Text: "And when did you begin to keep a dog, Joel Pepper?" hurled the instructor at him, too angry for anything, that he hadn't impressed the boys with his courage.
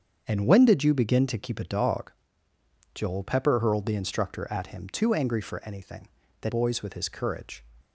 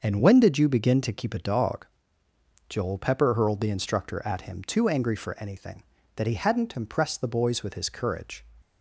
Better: second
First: starts louder than the rest; strong; until 1.2 s; 7 dB // skips "he hadn't impressed the"; at 6.4 s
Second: starts louder than the rest; until 1.0 s; 6 dB

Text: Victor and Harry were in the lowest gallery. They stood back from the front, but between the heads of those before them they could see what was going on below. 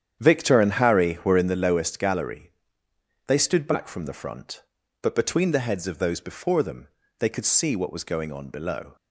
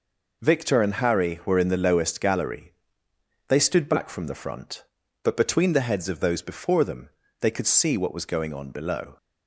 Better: second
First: starts louder than the rest; strong; until 1.5 s; 9 dB // pauses between "them" and "they"; slight; at 6.8 s; 0.32 s long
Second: pauses between "them" and "they"; slight; at 7.0 s; 0.32 s long

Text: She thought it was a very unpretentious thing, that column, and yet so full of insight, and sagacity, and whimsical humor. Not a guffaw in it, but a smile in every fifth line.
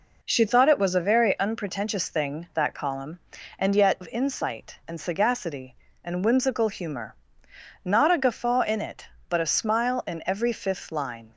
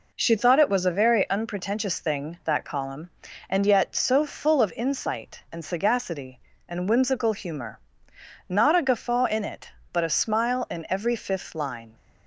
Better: second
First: skips "so full"; at 4.0 s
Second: none

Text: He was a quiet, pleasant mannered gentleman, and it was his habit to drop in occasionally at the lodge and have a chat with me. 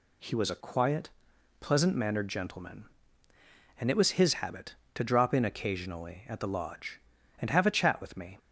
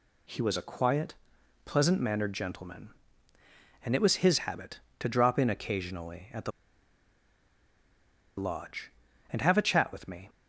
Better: first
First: none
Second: pauses between "the" and "lodge"; strong; at 6.5 s; 1.8 s long

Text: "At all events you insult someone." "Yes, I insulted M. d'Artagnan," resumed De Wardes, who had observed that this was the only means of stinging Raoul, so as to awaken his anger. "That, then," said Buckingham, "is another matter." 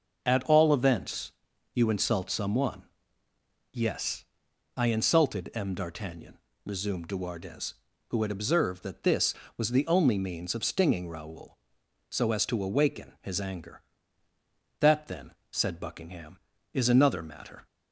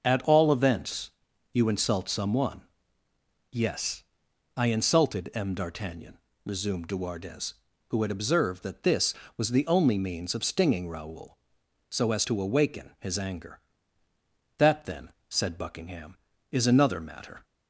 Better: neither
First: starts louder than the rest; noticeable; until 1.2 s; 6 dB // pauses between "events" and "you"; at 1.3 s; 0.42 s long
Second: starts louder than the rest; noticeable; until 1.0 s; 6 dB // pauses between "events" and "you"; at 1.0 s; 0.42 s long

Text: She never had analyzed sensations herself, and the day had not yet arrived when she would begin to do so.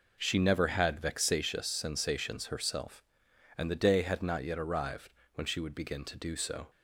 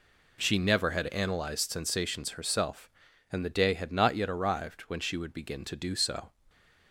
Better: second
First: says "vexatious" for "analyzed"; at 0.9 s // pauses between "arrived" and "when"; slight; at 5.0 s; 0.26 s long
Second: none

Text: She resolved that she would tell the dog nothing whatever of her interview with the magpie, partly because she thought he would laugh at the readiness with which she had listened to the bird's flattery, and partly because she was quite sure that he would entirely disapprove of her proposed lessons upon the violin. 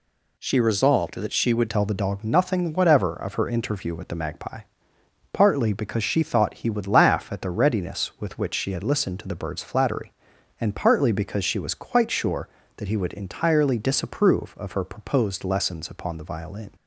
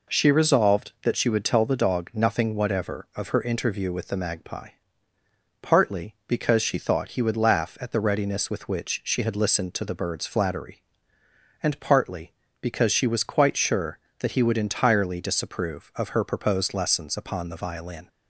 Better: second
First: changes voice at "tell"; from 1.6 s on; 15.1 s long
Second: none

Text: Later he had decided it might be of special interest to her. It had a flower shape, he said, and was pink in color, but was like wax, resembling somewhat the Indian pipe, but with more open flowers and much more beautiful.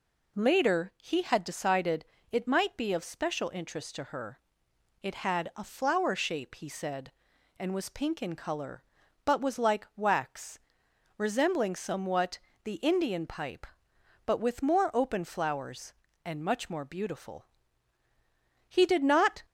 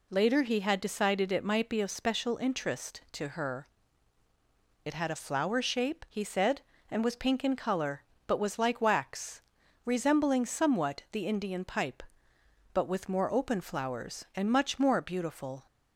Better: second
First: pauses between "decided" and "it"; slight; at 2.0 s; 0.26 s long // pauses between "somewhat" and "the"; slight; at 12.3 s; 0.26 s long // goes on to say "He did not"; noticeable; from 18.6 s on; 0.74 s long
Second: none

